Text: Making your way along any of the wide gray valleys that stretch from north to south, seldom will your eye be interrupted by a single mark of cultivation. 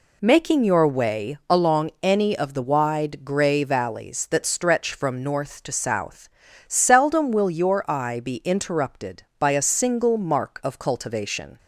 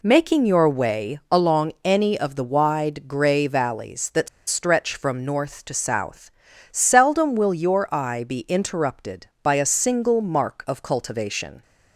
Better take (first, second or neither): first